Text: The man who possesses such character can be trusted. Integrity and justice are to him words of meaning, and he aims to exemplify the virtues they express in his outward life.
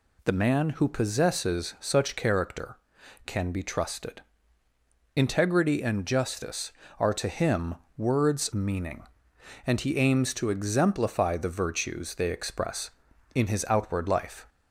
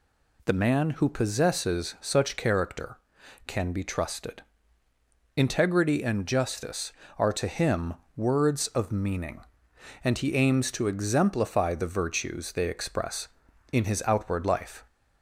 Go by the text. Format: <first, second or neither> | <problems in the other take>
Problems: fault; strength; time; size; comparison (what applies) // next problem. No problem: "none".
second | pauses between "him" and "words"; slight; at 7.7 s; 0.20 s long; slight in the second // skips "of"; at 8.5 s